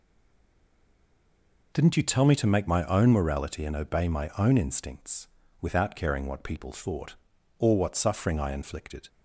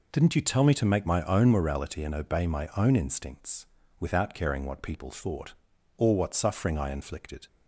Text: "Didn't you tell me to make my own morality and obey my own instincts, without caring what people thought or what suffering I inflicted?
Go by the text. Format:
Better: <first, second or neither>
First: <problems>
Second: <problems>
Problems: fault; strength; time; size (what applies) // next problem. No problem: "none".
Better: second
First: stays silent before the first word; noticeable; until 1.7 s; 1.7 s long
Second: none